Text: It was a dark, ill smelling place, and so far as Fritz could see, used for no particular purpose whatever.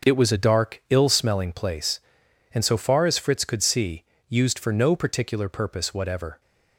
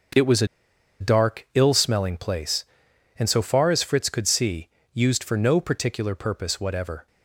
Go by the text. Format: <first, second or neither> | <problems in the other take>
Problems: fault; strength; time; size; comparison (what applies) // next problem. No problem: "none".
first | starts louder than the rest; until 1.7 s; 6 dB; also in the first // pauses between "a" and "dark"; noticeable; at 0.4 s; 0.53 s long